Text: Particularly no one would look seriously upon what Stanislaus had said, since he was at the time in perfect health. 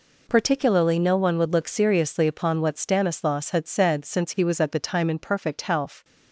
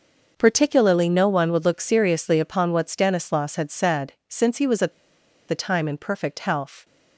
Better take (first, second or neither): first